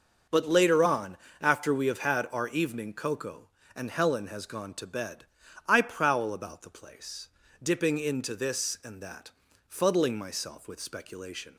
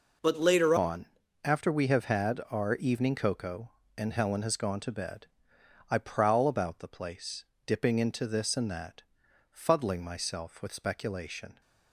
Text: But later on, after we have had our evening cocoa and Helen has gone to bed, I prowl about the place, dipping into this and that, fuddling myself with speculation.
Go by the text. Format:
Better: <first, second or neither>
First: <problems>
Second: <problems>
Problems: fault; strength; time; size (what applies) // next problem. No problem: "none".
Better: first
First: none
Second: changes voice at "on"; from 0.7 s on; 10.9 s long